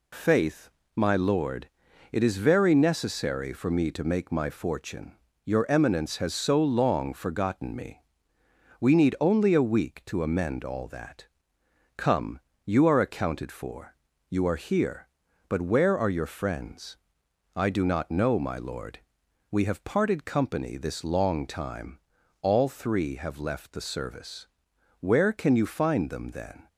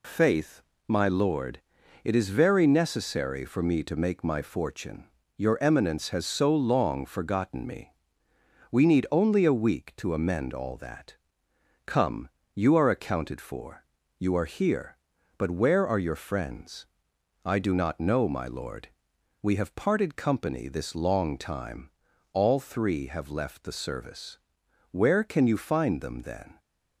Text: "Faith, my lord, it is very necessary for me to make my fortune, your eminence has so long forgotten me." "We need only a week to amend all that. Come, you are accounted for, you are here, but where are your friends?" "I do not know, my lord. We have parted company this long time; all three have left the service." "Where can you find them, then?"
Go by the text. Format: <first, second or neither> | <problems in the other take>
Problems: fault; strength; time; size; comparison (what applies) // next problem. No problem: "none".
neither | none